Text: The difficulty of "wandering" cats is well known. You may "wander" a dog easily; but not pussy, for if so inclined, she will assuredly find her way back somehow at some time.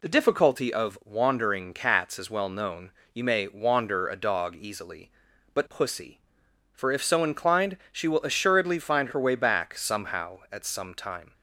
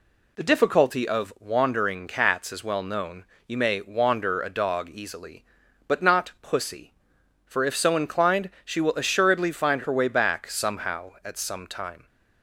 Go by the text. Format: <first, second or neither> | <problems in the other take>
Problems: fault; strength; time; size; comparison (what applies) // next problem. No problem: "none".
second | skips "not"; at 5.6 s